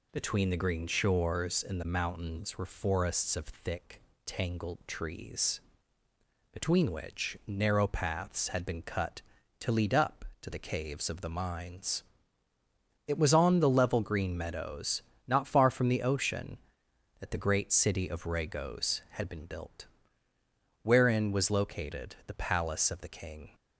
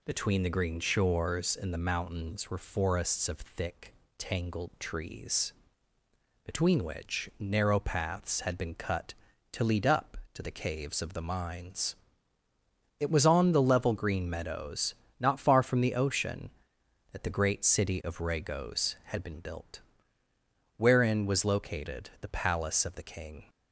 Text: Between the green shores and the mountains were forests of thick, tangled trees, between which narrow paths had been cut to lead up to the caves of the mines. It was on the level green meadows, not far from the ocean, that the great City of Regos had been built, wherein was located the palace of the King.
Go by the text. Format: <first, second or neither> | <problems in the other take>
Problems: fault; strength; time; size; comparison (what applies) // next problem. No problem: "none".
neither | none